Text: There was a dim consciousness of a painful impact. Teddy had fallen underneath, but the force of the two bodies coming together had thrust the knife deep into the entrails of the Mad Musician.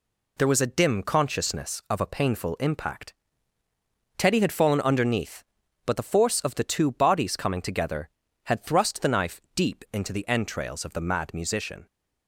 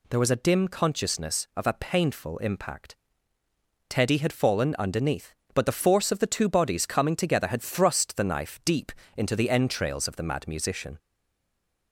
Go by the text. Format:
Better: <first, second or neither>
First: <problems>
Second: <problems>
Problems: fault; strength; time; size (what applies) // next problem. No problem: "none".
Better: first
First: none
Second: pauses between "deep" and "into"; slight; at 8.9 s; 0.24 s long // stays silent after the last word; slight; from 10.9 s on; 1.0 s long